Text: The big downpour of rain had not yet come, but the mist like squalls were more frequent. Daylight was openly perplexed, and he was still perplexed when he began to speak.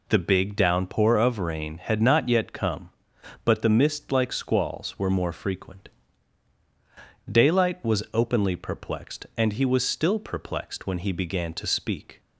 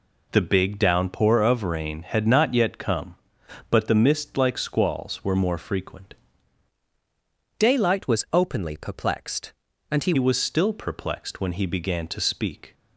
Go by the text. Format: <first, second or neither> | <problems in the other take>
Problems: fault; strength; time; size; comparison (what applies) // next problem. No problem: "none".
first | changes voice from "Daylight" to "he"; from 7.5 to 10.1 s; 2.6 s long